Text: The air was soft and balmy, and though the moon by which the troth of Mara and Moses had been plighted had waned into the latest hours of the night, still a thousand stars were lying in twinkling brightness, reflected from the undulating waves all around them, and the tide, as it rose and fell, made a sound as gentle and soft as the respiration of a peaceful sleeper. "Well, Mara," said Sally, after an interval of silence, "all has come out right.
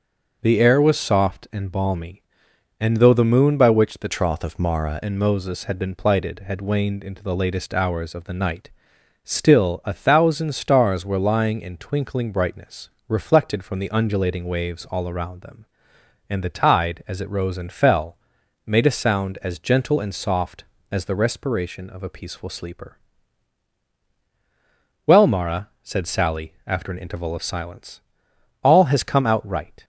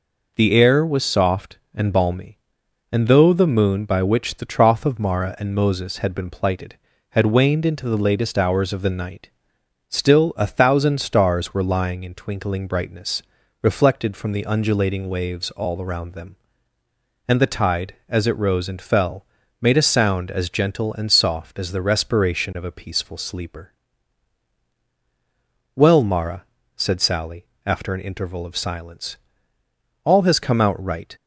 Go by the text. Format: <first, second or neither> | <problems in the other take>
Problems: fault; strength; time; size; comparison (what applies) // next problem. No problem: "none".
second | changes voice from "troth" to "Mara"; from 4.0 to 5.0 s; 1.0 s long